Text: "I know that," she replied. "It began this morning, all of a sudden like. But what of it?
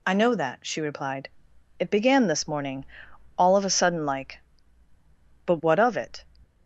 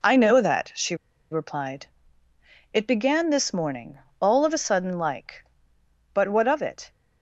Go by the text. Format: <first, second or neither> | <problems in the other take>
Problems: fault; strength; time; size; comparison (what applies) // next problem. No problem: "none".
first | pauses between "she" and "replied"; slight; at 0.9 s; 0.35 s long